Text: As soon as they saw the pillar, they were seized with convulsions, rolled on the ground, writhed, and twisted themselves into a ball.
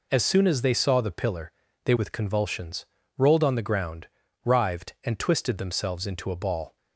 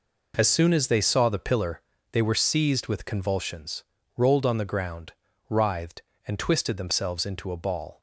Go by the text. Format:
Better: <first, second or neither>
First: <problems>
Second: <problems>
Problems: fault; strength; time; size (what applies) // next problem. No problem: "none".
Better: second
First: skips "were seized"; at 1.9 s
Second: none